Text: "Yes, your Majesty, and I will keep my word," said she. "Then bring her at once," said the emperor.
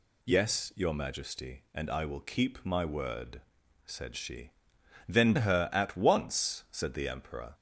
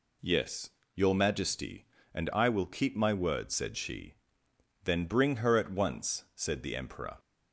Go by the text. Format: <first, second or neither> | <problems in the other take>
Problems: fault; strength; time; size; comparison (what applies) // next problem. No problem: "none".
second | skips "bring"; at 5.3 s